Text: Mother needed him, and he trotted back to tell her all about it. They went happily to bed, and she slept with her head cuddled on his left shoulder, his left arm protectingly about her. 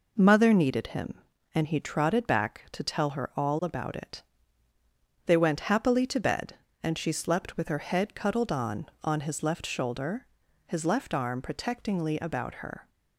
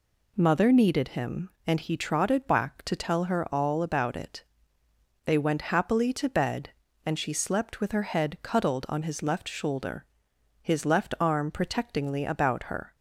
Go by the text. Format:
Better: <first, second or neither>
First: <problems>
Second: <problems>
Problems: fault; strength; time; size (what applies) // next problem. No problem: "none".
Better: second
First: says "on" twice; at 9.0 s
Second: none